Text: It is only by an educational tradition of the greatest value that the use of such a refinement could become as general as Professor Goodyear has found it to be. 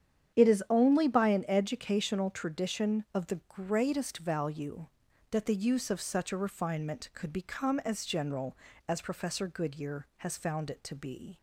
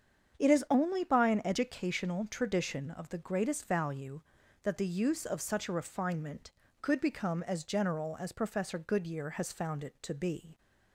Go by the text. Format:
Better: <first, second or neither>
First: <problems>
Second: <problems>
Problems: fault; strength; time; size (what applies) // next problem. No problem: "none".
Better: neither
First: starts louder than the rest; strong; until 1.3 s; 9 dB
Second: starts louder than the rest; strong; until 1.4 s; 7.5 dB